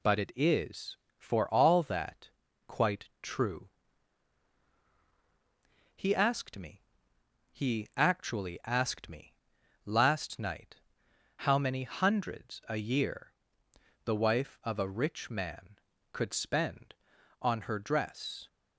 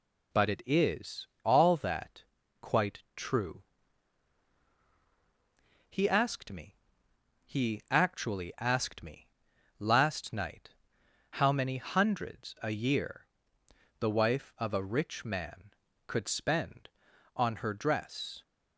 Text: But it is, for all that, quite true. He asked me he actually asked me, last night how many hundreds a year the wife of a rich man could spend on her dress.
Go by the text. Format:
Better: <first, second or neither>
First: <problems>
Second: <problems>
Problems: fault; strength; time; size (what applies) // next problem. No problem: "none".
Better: first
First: pauses between "me" and "he"; noticeable; at 6.7 s; 0.74 s long // pauses between "night" and "how"; noticeable; at 10.7 s; 0.56 s long // pauses between "year" and "the"; noticeable; at 13.3 s; 0.71 s long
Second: skips "for"; at 1.3 s // pauses between "me" and "he"; noticeable; at 6.7 s; 0.74 s long // pauses between "night" and "how"; noticeable; at 10.7 s; 0.56 s long // pauses between "year" and "the"; noticeable; at 13.2 s; 0.72 s long